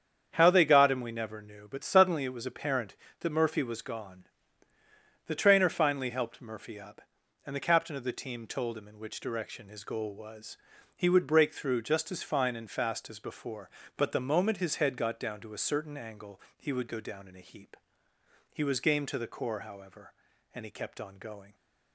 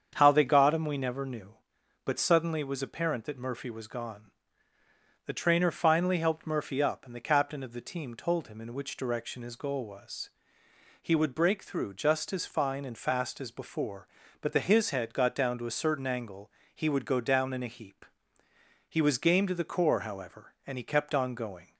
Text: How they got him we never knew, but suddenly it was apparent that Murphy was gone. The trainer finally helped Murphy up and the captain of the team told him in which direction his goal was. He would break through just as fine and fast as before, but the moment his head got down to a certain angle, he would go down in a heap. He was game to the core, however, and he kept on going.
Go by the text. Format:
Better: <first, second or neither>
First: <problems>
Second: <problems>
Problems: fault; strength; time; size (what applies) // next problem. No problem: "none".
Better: first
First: starts louder than the rest; strong; until 1.3 s; 8 dB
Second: starts louder than the rest; strong; until 1.1 s; 7.5 dB // skips "moment"; at 14.5 s